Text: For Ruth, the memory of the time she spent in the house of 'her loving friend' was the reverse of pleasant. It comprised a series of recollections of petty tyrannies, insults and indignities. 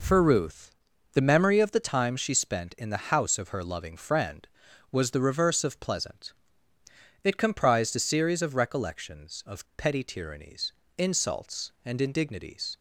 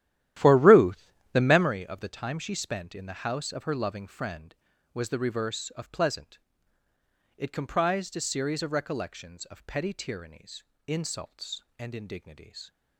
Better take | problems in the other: first | starts louder than the rest; strong; until 1.7 s; 12.5 dB

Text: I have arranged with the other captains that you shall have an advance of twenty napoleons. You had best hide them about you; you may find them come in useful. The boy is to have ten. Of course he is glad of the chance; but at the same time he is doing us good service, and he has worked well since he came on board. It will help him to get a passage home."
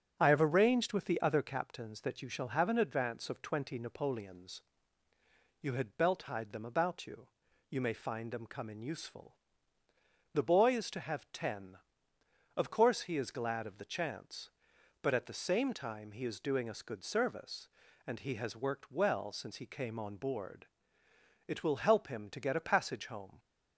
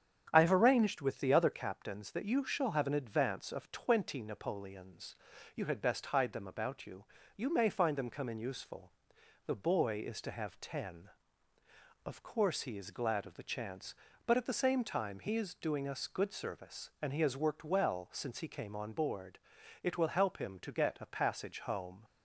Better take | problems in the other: second | starts louder than the rest; strong; until 1.2 s; 7.5 dB; strong in the second // says "belt" for "best"; at 5.9 s

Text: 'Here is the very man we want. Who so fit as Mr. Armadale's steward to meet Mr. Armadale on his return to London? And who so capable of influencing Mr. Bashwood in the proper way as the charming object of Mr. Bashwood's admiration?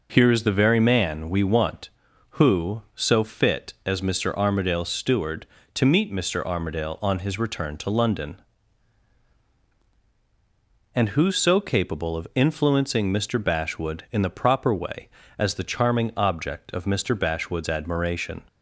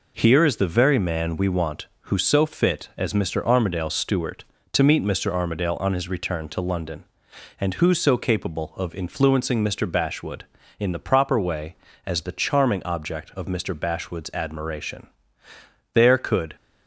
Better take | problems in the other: first | goes on to say "There could"; noticeable; from 15.9 s on; 0.62 s long

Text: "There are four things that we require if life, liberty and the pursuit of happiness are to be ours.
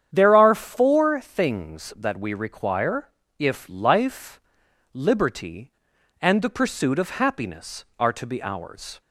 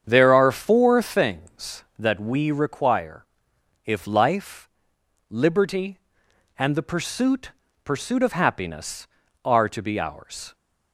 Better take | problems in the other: first | starts louder than the rest; strong; until 1.0 s; 8 dB; strong in the first // pauses between "require" and "if"; noticeable; at 3.2 s; 0.60 s long; slight in the first // says "pursuit" twice; at 7.8 s

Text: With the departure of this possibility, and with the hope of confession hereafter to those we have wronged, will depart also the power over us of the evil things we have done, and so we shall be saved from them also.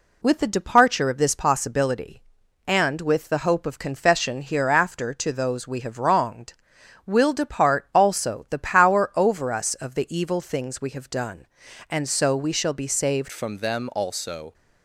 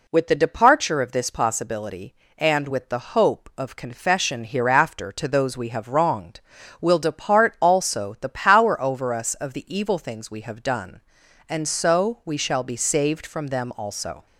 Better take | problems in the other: second | changes voice at "from"; from 13.3 s on; 1.2 s long

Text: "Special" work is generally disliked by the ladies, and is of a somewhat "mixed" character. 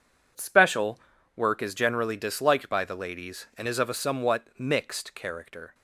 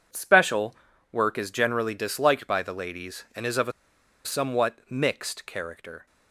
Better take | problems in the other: first | pauses between "Special" and "work"; at 0.7 s; 0.38 s long; also in the first // pauses between "a" and "somewhat"; noticeable; at 3.7 s; 0.53 s long

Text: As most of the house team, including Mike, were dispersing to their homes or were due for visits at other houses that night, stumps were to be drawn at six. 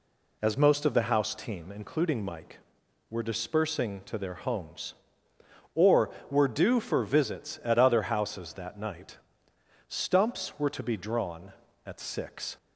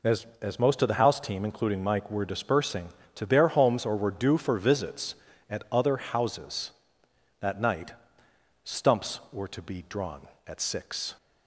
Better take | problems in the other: first | says "As" twice; at 0.4 s

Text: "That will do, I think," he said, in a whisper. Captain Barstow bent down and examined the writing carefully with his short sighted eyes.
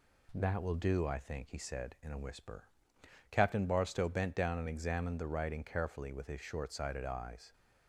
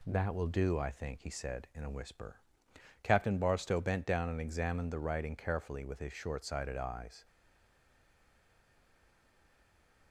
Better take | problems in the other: first | stays silent after the last word; strong; from 7.2 s on; 2.9 s long

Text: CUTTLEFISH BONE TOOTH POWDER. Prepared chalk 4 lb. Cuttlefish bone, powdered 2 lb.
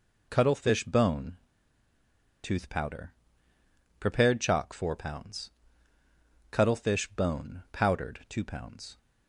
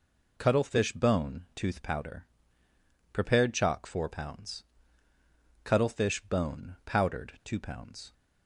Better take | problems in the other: second | pauses between "BONE" and "TOOTH"; at 1.3 s; 1.0 s long

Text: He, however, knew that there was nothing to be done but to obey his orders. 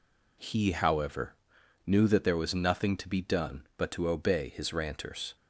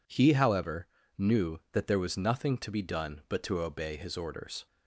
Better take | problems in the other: second | says "ranters" for "orders"; at 4.7 s

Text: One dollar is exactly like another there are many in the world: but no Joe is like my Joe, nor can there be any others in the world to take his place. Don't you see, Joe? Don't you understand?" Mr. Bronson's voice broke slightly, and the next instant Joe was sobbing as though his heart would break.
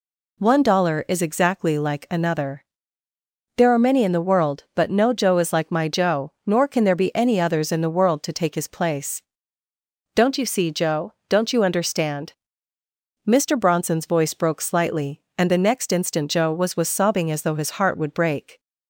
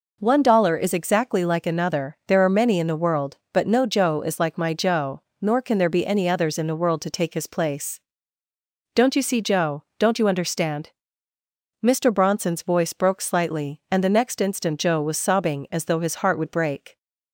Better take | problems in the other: second | pauses between "another" and "there"; noticeable; at 2.6 s; 0.92 s long // says "was" twice; at 16.7 s

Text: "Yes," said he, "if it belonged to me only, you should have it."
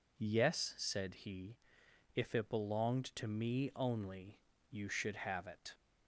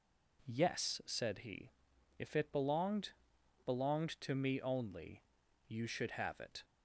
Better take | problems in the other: first | says "belonged" twice; at 3.6 s

